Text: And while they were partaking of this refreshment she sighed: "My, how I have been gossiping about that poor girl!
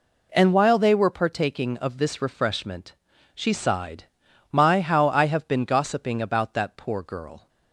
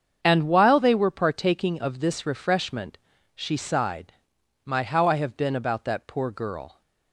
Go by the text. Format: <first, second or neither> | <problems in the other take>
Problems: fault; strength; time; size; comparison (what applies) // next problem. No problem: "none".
first | starts louder than the rest; strong; until 1.2 s; 7 dB // pauses between "refreshment" and "she"; at 2.9 s; 0.38 s long; also in the first // skips "gossiping"; at 5.5 s